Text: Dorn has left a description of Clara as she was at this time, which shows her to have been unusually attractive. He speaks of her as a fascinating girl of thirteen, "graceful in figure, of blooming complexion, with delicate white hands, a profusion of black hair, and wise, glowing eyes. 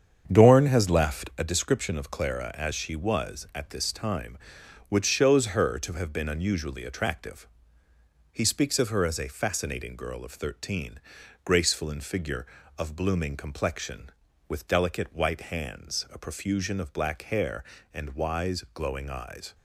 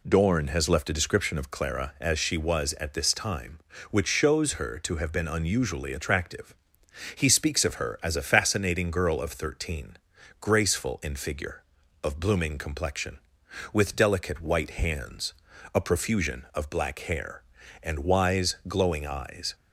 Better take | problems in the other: second | starts louder than the rest; strong; until 1.5 s; 7.5 dB

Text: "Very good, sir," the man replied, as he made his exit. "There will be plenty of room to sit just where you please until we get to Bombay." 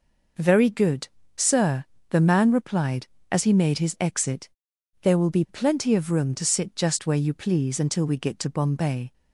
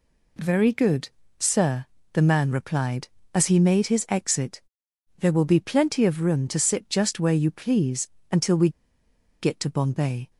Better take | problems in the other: first | pauses between "please" and "until"; slight; at 8.0 s; 0.24 s long // pauses between "we" and "get"; noticeable; at 8.6 s; 0.71 s long

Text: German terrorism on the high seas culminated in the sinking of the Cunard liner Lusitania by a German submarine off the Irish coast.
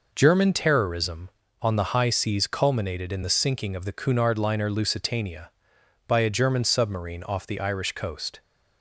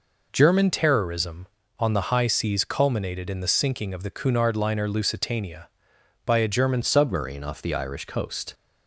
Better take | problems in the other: first | changes voice at "submarine"; from 6.8 s on; 1.7 s long

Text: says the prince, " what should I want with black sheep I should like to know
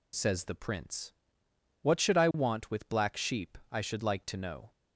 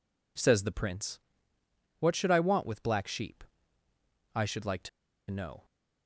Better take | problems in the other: first | pauses between "sheep" and "I"; noticeable; at 3.4 s; 0.92 s long; slight in the first // pauses between "to" and "know"; at 4.8 s; 0.41 s long

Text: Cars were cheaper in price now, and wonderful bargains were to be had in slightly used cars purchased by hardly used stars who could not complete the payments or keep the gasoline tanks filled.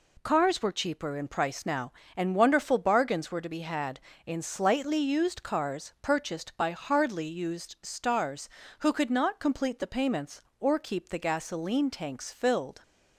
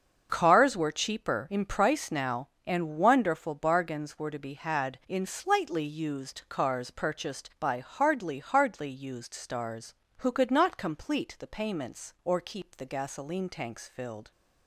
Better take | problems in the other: first | starts louder than the rest; until 1.3 s; 6.5 dB // says "hardly" twice; at 8.3 s

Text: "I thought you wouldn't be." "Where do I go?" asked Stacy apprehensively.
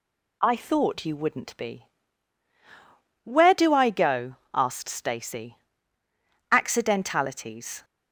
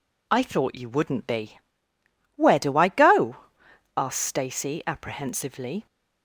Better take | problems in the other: second | says "accidentalities" for "apprehensively"; at 6.5 s

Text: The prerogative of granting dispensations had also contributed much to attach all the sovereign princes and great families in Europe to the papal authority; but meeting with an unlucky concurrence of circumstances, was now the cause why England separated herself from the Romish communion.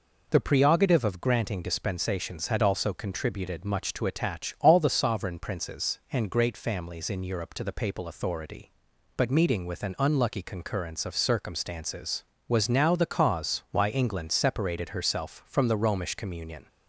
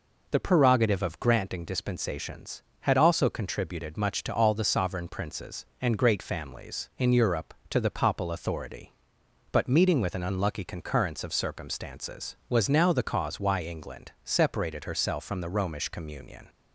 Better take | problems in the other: first | skips "attach"; at 4.3 s

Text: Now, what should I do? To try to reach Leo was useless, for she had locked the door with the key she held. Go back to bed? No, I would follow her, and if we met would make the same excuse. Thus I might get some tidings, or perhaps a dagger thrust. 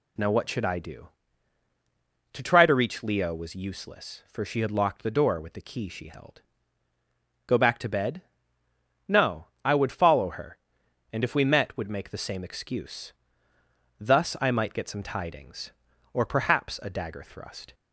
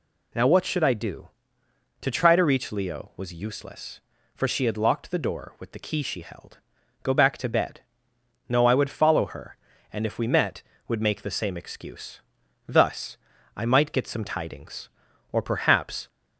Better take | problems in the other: first | pauses between "Thus" and "I"; at 13.1 s; 0.40 s long // stops before "a dagger thrust"; at 16.0 s

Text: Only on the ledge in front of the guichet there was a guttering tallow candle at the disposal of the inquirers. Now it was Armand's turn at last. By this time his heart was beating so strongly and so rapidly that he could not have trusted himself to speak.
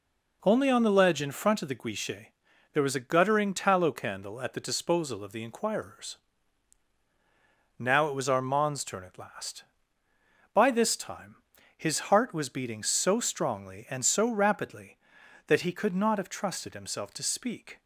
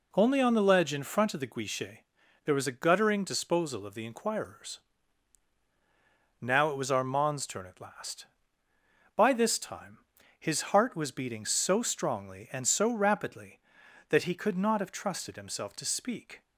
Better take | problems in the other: first | pauses between "guichet" and "there"; at 1.9 s; 0.44 s long; also in the first // skips "tallow candle at the"; at 3.2 s // pauses between "time" and "his"; at 9.9 s; 0.40 s long; also in the first

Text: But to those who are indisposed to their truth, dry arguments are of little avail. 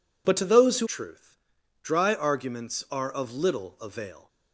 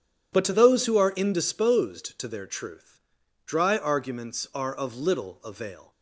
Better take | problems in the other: second | skips "are indisposed to their"; at 0.8 s

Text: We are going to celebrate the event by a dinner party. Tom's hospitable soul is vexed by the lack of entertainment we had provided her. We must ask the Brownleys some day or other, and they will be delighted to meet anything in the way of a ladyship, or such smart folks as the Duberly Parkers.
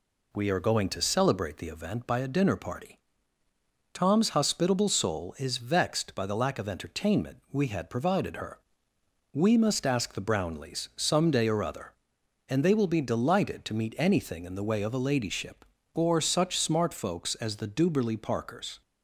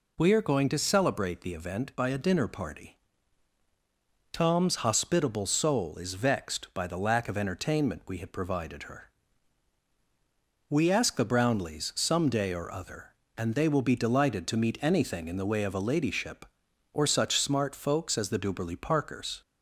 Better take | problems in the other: first | skips "must"; at 10.8 s

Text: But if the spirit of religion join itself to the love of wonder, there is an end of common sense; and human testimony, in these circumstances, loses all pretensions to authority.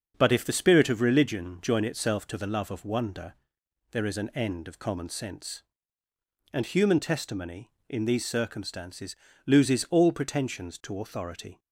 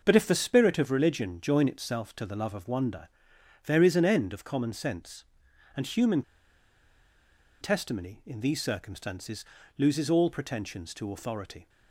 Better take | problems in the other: first | starts louder than the rest; noticeable; until 1.0 s; 6 dB; also in the first // pauses between "human" and "testimony"; strong; at 6.2 s; 1.3 s long

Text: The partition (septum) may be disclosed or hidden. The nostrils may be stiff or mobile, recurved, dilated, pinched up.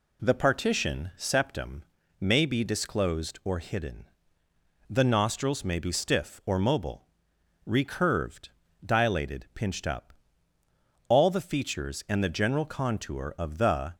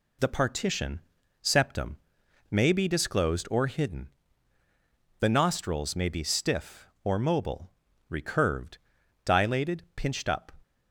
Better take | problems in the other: second | goes on to say "All the features and the general contour of the"; strong; from 11.0 s on; 2.8 s long

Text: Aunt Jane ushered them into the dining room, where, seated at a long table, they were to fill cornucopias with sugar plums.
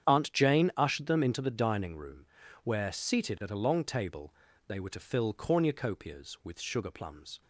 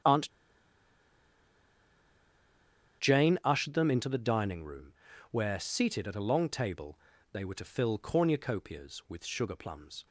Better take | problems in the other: first | starts louder than the rest; strong; until 3.8 s; 9 dB; strong in the first // pauses between "Aunt" and "Jane"; strong; at 0.2 s; 2.7 s long

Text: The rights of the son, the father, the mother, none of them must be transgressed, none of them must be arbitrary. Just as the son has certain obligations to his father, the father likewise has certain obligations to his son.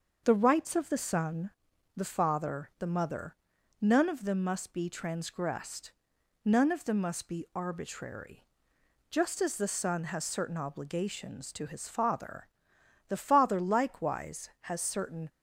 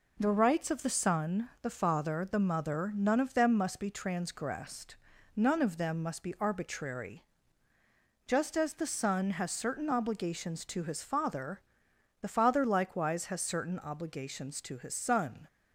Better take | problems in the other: second | starts louder than the rest; until 1.2 s; 6.5 dB // stops before "obligations to his son"; at 15.2 s

